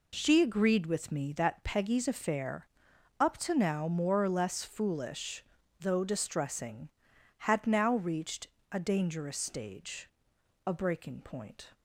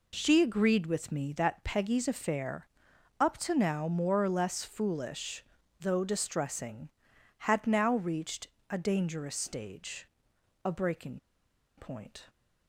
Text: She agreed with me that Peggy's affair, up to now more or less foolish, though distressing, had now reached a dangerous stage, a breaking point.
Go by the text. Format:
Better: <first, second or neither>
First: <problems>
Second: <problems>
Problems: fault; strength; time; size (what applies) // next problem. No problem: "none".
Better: first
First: pauses between "reached" and "a"; slight; at 8.4 s; 0.25 s long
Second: pauses between "reached" and "a"; slight; at 8.4 s; 0.24 s long // pauses between "breaking" and "point"; noticeable; at 11.1 s; 0.59 s long